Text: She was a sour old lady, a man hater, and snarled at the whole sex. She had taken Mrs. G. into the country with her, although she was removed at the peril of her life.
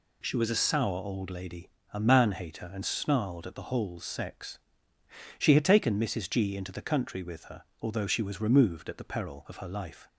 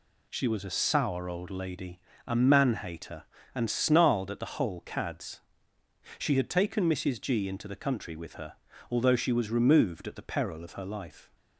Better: first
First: none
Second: says "cads" for "sex"; at 4.8 s

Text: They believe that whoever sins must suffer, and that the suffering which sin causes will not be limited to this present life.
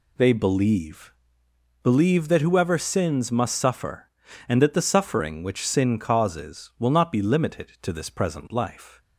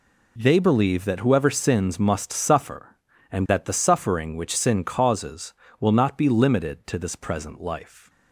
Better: second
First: says "believe" twice; at 1.8 s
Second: none

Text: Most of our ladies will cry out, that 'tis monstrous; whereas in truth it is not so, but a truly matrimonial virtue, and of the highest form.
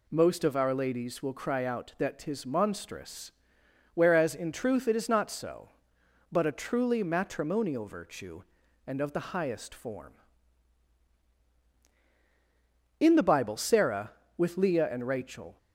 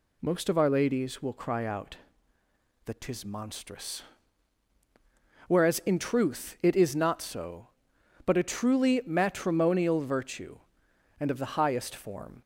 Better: second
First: goes on to say "In the Bible Sarah with Leah and Rachel"; strong; from 13.0 s on; 2.5 s long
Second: none

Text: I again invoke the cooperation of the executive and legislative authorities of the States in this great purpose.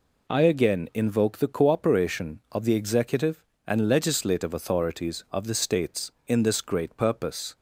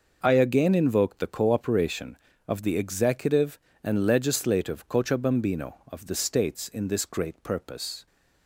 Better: first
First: none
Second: says "cochabambino" for "authorities"; at 4.8 s

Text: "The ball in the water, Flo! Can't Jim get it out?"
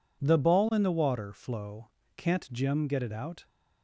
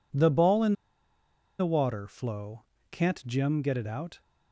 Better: first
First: none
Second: pauses between "in" and "the"; noticeable; at 0.7 s; 0.87 s long

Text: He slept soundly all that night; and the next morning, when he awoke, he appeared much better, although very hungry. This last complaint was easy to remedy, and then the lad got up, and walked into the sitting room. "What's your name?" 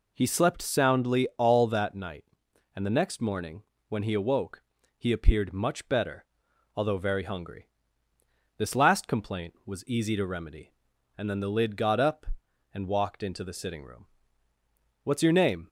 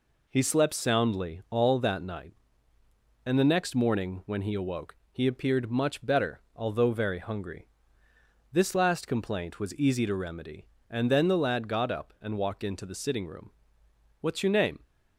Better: second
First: says "lid" for "lad"; at 11.5 s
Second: none

